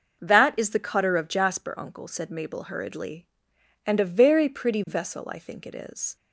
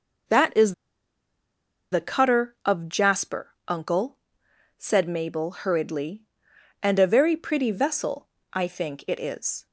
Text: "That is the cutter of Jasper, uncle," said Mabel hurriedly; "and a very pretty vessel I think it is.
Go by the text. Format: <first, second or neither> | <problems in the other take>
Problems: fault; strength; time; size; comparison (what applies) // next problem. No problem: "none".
first | pauses between "is" and "the"; at 0.7 s; 1.1 s long // pauses between "vessel" and "I"; slight; at 8.2 s; 0.26 s long